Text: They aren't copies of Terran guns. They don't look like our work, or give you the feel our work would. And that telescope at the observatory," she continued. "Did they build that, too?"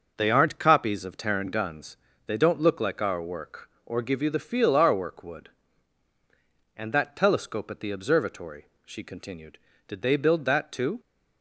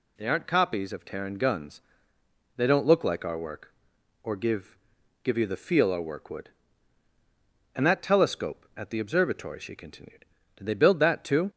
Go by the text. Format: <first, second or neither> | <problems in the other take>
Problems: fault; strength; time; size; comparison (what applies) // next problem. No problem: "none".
first | says "give" twice; at 5.2 s